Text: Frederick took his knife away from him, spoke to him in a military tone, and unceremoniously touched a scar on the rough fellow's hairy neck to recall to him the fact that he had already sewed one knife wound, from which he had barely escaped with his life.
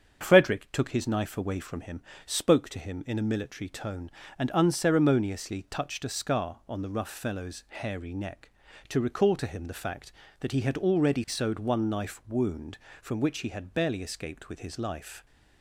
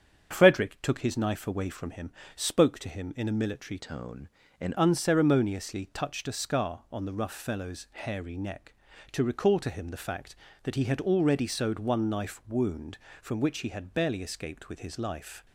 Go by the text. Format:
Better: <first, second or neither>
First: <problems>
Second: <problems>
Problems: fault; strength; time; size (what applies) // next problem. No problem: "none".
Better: first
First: starts louder than the rest; strong; until 1.2 s; 7.5 dB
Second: starts louder than the rest; strong; until 1.3 s; 7.5 dB // changes voice from "tone" to "and"; from 3.7 to 4.7 s; 1.0 s long